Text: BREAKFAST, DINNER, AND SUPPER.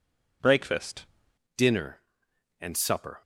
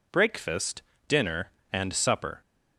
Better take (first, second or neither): second